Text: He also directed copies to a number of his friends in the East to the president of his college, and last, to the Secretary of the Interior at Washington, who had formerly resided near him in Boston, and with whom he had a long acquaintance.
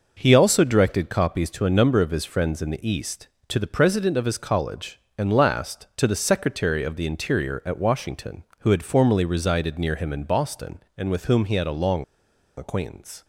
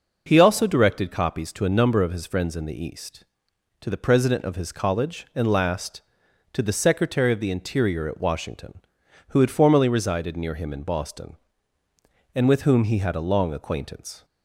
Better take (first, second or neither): second